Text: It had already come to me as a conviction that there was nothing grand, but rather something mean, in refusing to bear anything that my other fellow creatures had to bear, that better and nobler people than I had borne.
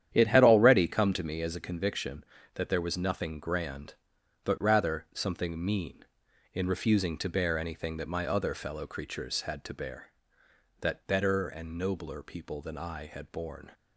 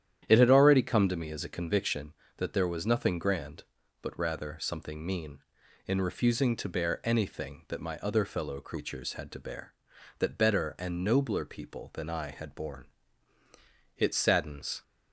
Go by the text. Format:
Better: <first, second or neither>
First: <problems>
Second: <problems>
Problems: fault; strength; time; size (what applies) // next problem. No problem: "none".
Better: first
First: starts louder than the rest; strong; until 1.1 s; 10 dB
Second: starts louder than the rest; strong; until 1.2 s; 10 dB // goes on to say "It saddens"; noticeable; from 13.9 s on; 0.84 s long